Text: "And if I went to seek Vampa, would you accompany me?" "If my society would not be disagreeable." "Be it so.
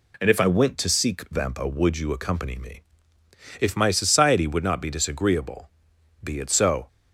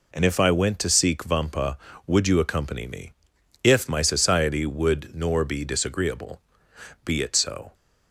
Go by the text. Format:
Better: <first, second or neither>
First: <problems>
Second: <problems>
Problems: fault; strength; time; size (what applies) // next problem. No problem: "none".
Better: first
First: none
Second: says "nor" for "not"; at 5.1 s